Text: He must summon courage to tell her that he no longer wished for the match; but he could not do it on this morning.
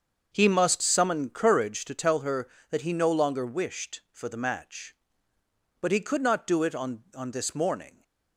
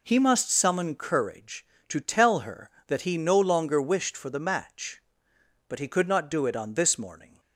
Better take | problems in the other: second | starts louder than the rest; until 1.3 s; 6.5 dB // says "on" twice; at 7.1 s

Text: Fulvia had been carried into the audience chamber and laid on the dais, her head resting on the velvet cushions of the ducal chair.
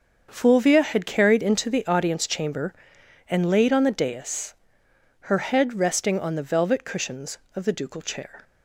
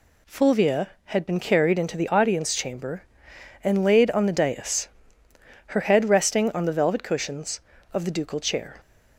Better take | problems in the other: second | starts louder than the rest; until 1.3 s; 6.5 dB // skips "been"; at 1.0 s

